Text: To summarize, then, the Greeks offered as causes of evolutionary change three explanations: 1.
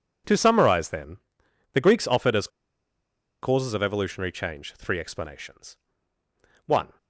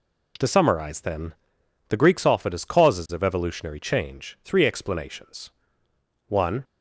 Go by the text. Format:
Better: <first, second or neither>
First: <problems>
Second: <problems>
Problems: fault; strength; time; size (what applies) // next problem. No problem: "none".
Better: second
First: pauses between "as" and "causes"; noticeable; at 2.4 s; 0.94 s long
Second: none